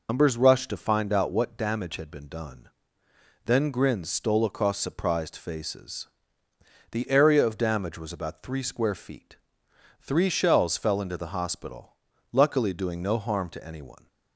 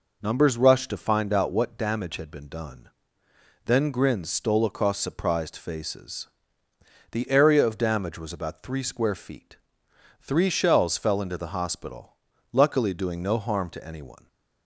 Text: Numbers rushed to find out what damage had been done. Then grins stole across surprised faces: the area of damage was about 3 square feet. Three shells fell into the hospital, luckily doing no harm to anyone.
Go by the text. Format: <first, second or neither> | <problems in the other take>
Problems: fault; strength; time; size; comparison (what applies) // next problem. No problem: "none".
second | loses the start of "Numbers"; at 0.0 s; 75 ms